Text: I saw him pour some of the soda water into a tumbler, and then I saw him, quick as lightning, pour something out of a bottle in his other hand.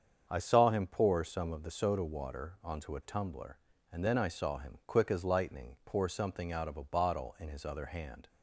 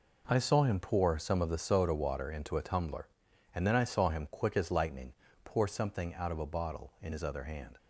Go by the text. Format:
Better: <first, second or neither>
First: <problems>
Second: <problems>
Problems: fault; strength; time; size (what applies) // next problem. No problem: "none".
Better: second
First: starts louder than the rest; strong; until 1.2 s; 7 dB // says "onto" for "into"; at 2.6 s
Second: none